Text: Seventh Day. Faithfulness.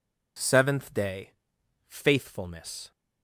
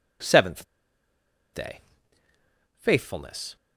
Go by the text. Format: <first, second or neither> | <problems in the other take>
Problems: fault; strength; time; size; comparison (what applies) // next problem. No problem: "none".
first | pauses between "Seventh" and "Day"; noticeable; at 0.6 s; 0.90 s long